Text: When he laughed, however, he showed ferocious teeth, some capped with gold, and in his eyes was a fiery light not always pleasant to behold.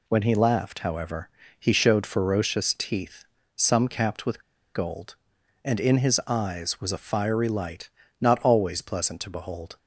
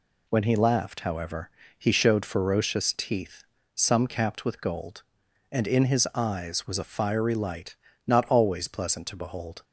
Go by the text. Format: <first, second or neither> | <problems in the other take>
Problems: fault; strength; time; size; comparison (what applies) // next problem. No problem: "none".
second | pauses between "with" and "gold"; slight; at 4.4 s; 0.32 s long // pauses between "light" and "not"; slight; at 7.8 s; 0.30 s long; slight in the second